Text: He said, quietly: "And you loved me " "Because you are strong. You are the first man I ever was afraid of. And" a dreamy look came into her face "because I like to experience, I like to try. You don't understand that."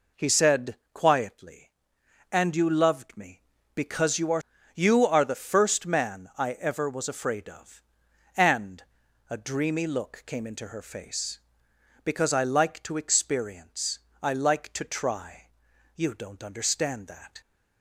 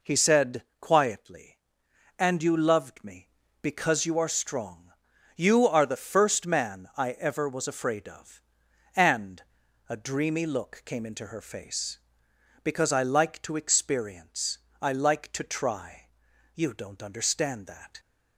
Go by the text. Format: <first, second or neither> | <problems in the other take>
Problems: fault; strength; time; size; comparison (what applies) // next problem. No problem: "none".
second | skips "strong"; at 4.5 s // pauses between "And" and "a"; noticeable; at 8.8 s; 0.48 s long; noticeable in the second